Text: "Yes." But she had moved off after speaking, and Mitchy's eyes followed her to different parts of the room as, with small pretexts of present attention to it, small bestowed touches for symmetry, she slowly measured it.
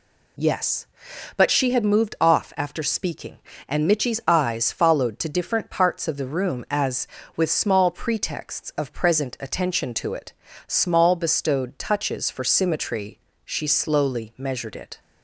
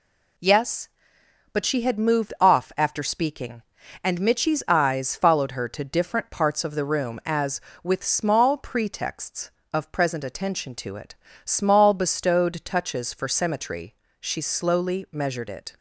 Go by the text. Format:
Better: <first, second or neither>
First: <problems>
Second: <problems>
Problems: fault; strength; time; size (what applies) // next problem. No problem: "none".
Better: second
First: skips "her"; at 5.1 s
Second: none